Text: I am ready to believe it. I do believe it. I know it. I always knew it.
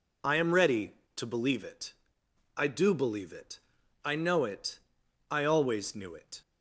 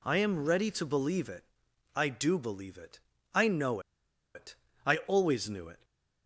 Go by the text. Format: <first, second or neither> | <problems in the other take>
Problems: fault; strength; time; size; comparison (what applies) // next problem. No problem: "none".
first | pauses between "know" and "it"; noticeable; at 3.7 s; 0.55 s long // stays silent after the last word; slight; from 5.7 s on; 0.5 s long